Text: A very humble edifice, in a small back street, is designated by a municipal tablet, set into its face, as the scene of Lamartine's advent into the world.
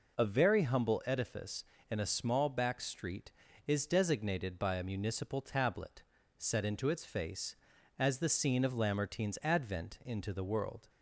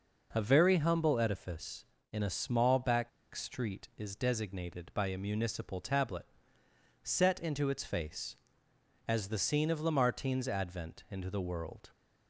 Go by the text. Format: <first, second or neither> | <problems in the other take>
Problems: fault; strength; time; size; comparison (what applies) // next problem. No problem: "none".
first | pauses between "back" and "street"; slight; at 3.0 s; 0.24 s long